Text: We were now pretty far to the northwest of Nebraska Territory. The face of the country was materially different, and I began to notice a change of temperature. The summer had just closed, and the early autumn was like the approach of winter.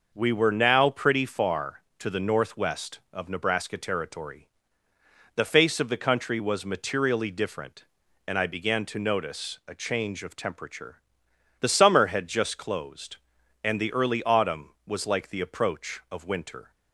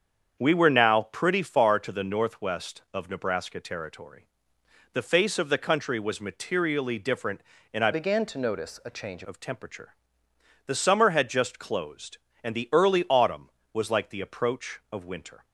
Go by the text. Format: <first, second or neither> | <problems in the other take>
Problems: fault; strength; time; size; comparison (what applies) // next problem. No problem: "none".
first | starts louder than the rest; strong; until 1.5 s; 7.5 dB // changes voice from "began" to "change"; from 7.9 to 9.2 s; 1.3 s long